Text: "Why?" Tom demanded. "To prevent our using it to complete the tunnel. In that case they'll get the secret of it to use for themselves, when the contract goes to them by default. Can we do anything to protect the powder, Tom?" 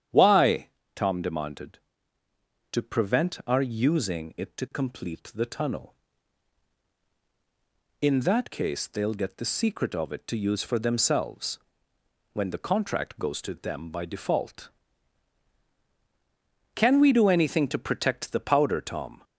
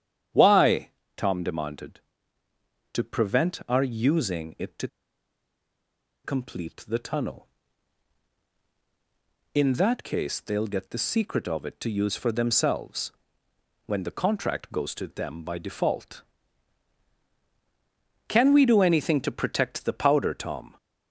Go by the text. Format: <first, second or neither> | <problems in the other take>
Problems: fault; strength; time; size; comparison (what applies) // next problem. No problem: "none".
first | starts louder than the rest; strong; until 1.5 s; 9.5 dB; strong in the first // pauses between "to" and "complete"; strong; at 4.8 s; 1.3 s long